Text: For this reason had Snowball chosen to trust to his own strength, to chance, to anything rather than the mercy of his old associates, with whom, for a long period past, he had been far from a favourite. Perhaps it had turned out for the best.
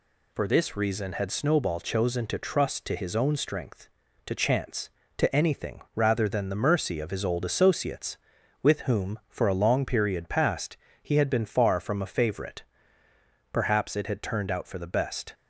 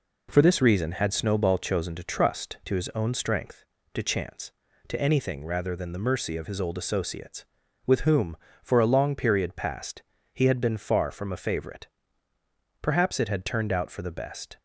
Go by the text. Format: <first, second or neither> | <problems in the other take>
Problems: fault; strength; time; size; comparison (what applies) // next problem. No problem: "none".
neither | none